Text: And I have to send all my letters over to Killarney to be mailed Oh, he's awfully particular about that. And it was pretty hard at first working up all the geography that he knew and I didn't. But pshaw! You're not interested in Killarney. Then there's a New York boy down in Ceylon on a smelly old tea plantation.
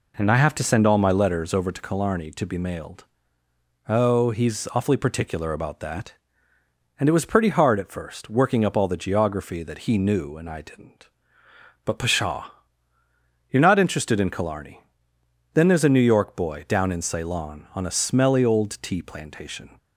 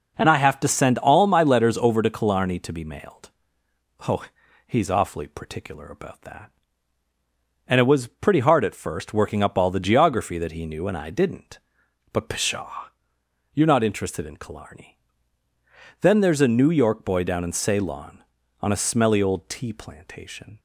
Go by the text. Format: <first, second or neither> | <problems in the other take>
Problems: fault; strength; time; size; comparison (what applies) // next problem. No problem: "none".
neither | pauses between "mailed" and "Oh"; noticeable; the same in both